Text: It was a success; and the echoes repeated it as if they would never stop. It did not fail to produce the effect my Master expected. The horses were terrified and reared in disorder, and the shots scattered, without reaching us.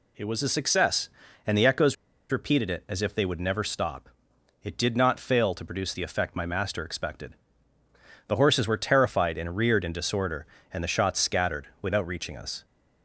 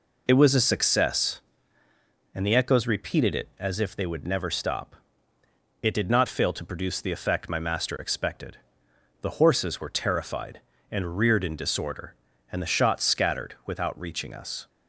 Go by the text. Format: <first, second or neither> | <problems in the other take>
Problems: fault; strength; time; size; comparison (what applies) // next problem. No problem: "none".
second | pauses between "echoes" and "repeated"; at 1.9 s; 0.37 s long